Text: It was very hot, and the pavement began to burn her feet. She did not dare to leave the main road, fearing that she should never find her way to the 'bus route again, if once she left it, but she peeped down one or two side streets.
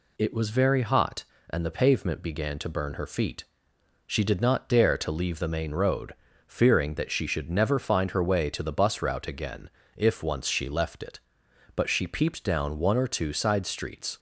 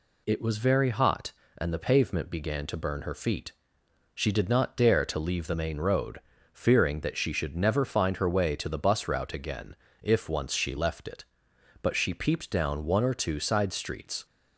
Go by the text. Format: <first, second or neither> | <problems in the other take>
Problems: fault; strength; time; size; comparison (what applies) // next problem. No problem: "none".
neither | none